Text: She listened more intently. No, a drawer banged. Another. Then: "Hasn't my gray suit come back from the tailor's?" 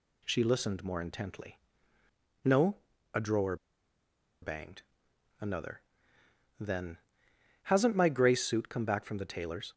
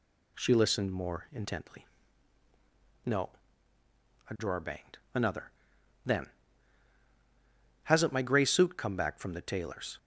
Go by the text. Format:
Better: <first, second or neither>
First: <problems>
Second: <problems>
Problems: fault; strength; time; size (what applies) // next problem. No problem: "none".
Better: second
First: pauses between "drawer" and "banged"; noticeable; at 3.5 s; 0.85 s long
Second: none